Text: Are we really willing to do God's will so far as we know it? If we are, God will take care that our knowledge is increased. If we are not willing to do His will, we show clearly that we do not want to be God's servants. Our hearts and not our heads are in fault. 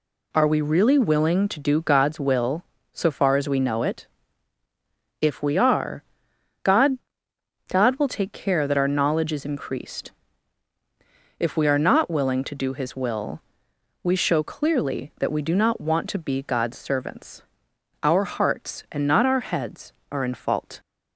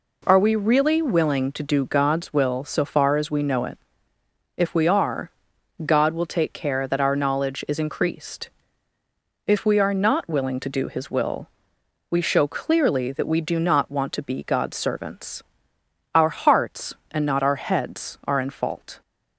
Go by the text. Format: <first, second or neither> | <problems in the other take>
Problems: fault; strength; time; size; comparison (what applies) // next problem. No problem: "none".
second | says "God" twice; at 7.6 s